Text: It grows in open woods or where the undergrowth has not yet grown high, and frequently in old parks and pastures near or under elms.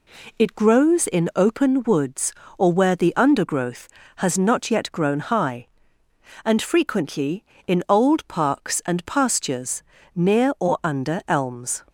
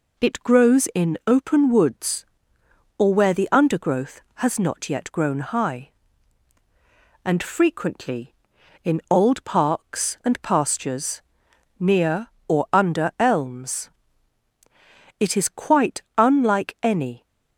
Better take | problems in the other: first | pauses between "pastures" and "near"; noticeable; at 11.2 s; 0.58 s long; slight in the first // goes on to say "It is quite unlike any"; strong; from 15.1 s on; 2.0 s long

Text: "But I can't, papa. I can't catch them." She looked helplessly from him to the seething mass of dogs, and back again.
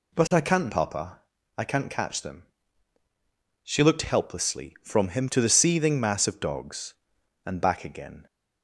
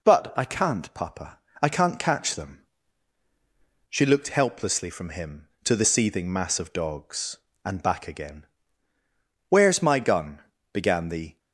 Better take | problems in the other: first | goes on to say "Where's my gun began the"; strong; from 9.4 s on; 1.8 s long

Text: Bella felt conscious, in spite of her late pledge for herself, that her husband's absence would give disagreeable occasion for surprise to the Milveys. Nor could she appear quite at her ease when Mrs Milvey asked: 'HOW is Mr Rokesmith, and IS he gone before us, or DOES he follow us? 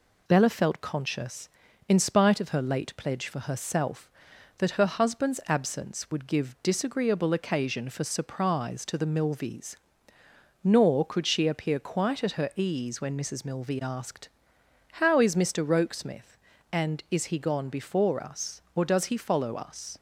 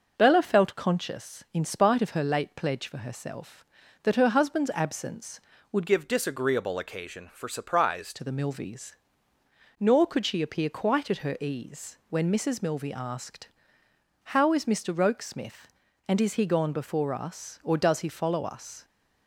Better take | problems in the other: first | starts louder than the rest; until 1.1 s; 6 dB // changes voice from "give" to "surprise"; from 5.8 to 8.1 s; 2.3 s long

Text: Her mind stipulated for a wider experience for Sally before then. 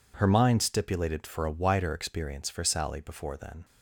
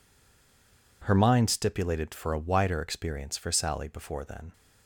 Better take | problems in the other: first | stays silent before the first word; until 1.0 s; 1.0 s long

